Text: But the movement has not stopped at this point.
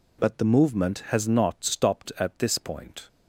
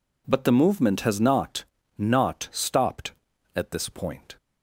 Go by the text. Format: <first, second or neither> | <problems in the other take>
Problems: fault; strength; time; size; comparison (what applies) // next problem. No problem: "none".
first | says "not" twice; at 1.9 s